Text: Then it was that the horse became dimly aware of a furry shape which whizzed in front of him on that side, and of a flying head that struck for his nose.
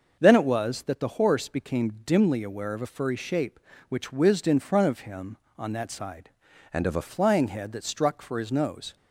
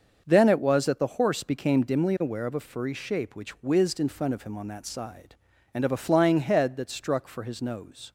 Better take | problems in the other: second | starts louder than the rest; noticeable; until 1.2 s; 6 dB; also in the second // changes voice from "and" to "a"; from 6.7 to 7.0 s; 0.3 s long

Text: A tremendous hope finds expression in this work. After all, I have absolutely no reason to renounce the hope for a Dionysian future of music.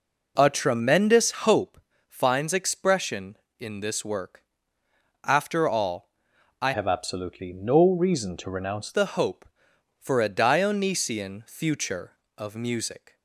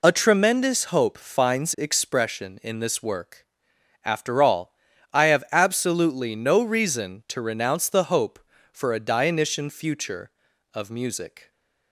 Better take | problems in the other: second | pauses between "hope" and "finds"; slight; at 1.8 s; 0.28 s long // changes voice from "have" to "renounce"; from 6.7 to 8.9 s; 2.2 s long

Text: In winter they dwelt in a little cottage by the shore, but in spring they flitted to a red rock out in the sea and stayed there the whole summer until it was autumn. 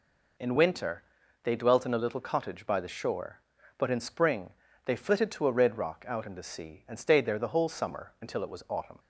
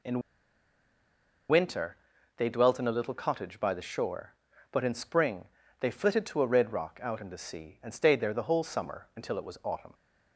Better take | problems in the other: first | pauses between "In" and "winter"; strong; at 0.2 s; 1.2 s long // pauses between "winter" and "they"; at 1.9 s; 0.42 s long; also in the first // pauses between "spring" and "they"; slight; at 5.4 s; 0.34 s long; slight in the first

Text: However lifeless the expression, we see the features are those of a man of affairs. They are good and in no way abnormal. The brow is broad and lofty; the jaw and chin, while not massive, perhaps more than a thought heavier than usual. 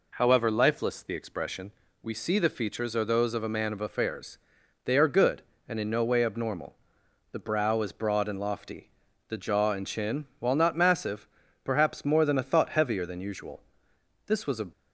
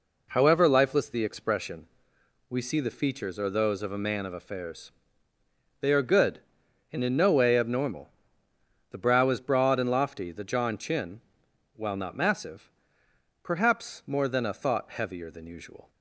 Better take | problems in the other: second | goes on to say "This was a"; slight; from 14.2 s on; 0.40 s long

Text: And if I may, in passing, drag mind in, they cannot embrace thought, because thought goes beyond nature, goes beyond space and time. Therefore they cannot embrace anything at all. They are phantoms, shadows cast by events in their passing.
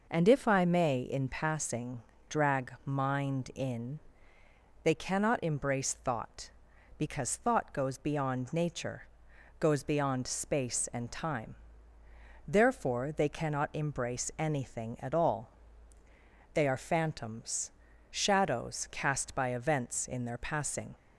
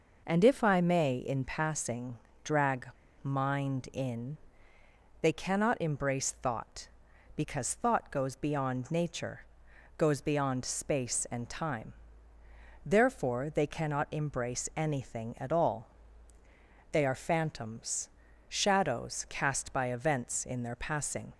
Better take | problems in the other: first | pauses between "drag" and "mind"; slight; at 2.8 s; 0.35 s long

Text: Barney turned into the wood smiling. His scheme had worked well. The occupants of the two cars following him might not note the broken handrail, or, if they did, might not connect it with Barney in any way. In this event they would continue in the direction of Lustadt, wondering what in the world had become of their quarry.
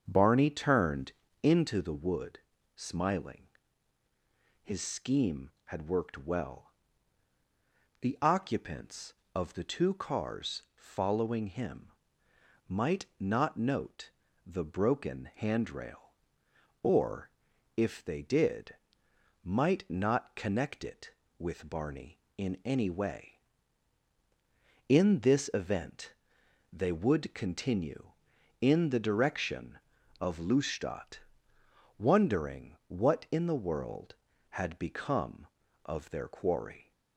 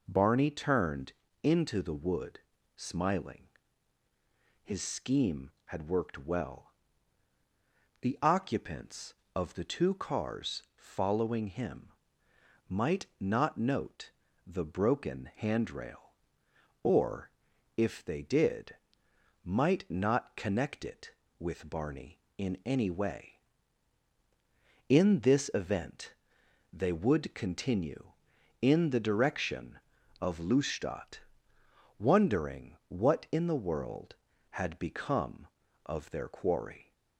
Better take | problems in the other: second | starts louder than the rest; until 1.9 s; 7 dB // pauses between "turned" and "into"; slight; at 1.1 s; 0.30 s long; slight in the second // pauses between "wood" and "smiling"; at 2.3 s; 0.38 s long; also in the second // pauses between "him" and "might"; noticeable; at 11.8 s; 0.80 s long; noticeable in the second // pauses between "note" and "the"; slight; at 14.0 s; 0.36 s long; slight in the second // pauses between "event" and "they"; noticeable; at 26.1 s; 0.58 s long; noticeable in the second

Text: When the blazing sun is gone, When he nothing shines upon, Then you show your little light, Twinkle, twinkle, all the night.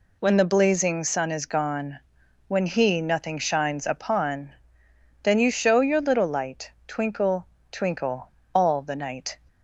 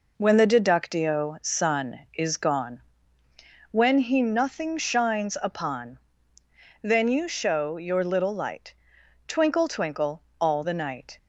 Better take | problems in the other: first | says "deductio" for "blazing"; at 0.4 s

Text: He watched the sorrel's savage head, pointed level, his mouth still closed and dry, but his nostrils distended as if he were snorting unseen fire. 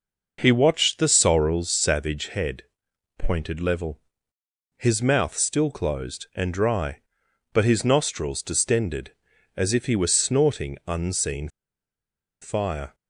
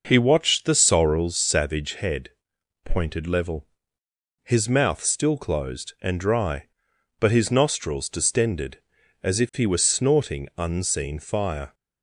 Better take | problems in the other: second | pauses between "unseen" and "fire"; noticeable; at 11.4 s; 0.92 s long

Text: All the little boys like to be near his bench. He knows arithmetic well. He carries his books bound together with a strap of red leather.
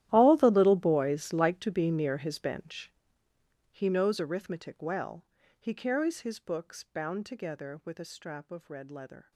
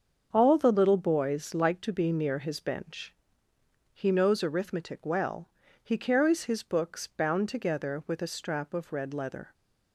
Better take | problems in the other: second | gets quieter; strong; throughout; 20 dB // starts louder than the rest; strong; until 1.1 s; 13 dB; also in the second

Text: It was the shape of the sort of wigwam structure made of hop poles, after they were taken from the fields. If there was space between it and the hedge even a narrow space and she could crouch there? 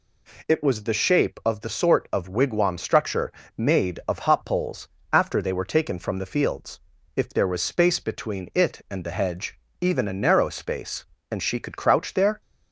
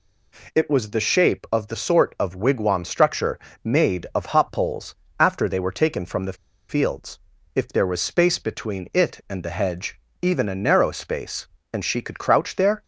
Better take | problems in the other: first | pauses between "structure" and "made"; slight; at 3.3 s; 0.26 s long; slight in the first // pauses between "the" and "fields"; slight; at 6.3 s; 0.34 s long // pauses between "hedge" and "even"; slight; at 9.9 s; 0.22 s long; slight in the first

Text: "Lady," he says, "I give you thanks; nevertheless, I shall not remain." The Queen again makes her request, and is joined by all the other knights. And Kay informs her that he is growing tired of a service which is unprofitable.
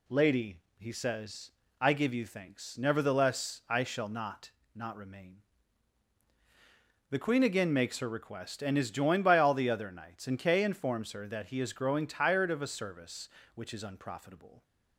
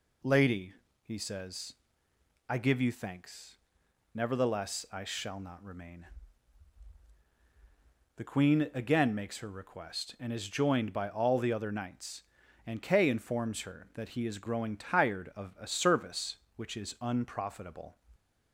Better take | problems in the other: second | says "not" twice; at 4.7 s

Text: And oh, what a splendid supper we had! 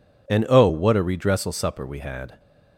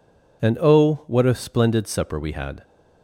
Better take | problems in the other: second | says "redressal" for "splendid"; at 1.0 s

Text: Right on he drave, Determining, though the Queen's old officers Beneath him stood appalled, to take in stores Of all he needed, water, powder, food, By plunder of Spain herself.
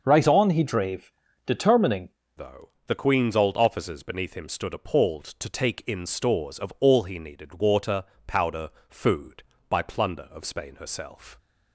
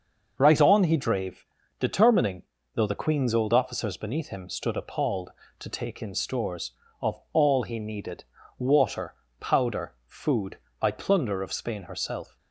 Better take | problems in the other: second | starts louder than the rest; noticeable; until 1.0 s; 6 dB; noticeable in the second // changes voice at "though"; from 2.3 s on; 9.0 s long // pauses between "though" and "the"; slight; at 2.6 s; 0.16 s long

